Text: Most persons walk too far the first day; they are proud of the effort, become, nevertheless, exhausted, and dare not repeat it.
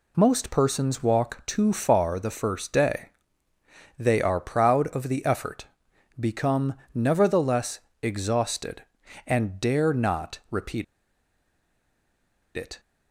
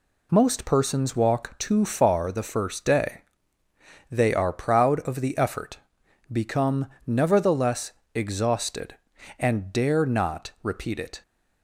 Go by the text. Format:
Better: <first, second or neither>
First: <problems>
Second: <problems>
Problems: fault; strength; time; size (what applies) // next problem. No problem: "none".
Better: second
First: pauses between "repeat" and "it"; strong; at 10.8 s; 1.7 s long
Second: none